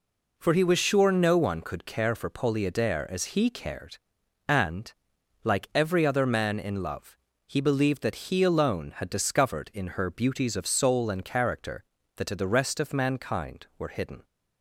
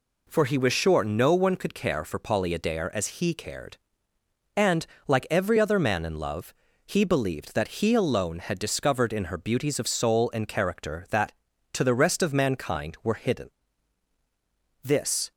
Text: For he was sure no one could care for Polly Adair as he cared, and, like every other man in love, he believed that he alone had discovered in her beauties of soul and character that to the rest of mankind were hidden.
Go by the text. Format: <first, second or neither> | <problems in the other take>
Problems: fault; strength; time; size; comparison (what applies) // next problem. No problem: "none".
first | goes on to say "This"; slight; from 14.8 s on; 0.48 s long